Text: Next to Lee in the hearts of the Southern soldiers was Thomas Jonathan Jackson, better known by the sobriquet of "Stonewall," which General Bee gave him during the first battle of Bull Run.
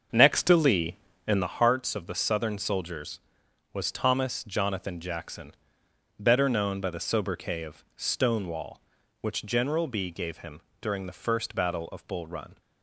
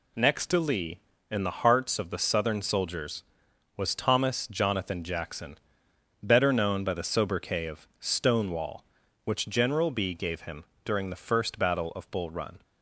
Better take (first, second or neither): second